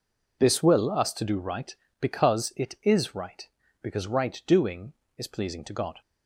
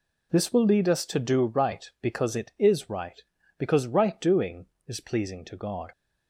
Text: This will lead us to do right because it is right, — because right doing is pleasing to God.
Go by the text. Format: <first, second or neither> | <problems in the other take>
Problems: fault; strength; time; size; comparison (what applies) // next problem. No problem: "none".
second | skips "lead"; at 0.9 s